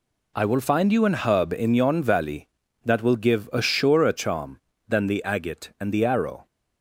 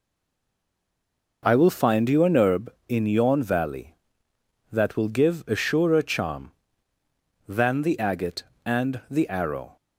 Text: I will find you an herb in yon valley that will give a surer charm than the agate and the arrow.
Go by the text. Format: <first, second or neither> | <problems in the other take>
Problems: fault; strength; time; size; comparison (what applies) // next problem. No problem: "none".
first | stays silent before the first word; noticeable; until 1.4 s; 1.4 s long